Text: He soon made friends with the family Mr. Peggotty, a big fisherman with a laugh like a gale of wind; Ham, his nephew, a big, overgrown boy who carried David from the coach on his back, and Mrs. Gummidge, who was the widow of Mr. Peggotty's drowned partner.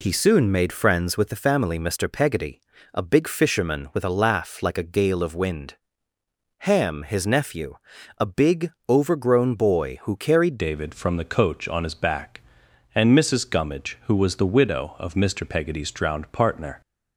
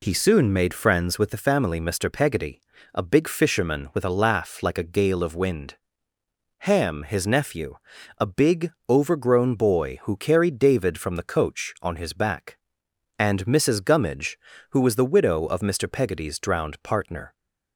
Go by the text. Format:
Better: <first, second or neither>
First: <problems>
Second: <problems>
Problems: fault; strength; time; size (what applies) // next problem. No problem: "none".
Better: second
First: changes voice at "David"; from 10.5 s on; 6.3 s long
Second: none